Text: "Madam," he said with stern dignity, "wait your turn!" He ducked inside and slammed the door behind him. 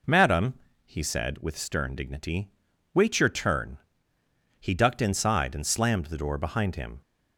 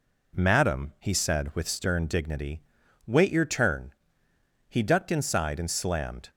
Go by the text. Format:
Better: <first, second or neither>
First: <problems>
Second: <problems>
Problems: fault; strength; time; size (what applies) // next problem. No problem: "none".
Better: first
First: none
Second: stops before "the door behind him"; at 6.2 s